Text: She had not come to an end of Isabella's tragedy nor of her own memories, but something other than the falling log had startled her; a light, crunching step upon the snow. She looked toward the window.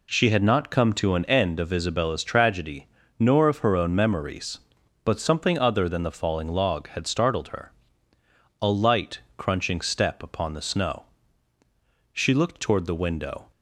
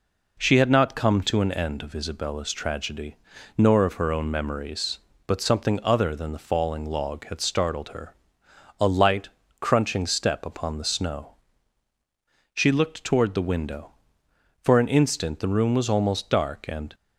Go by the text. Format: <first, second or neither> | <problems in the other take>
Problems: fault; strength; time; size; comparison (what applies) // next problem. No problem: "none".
first | pauses between "tragedy" and "nor"; at 3.1 s; 0.40 s long; slight in the first // goes on to say "For an instant the room was almost dark and"; strong; from 14.6 s on; 2.3 s long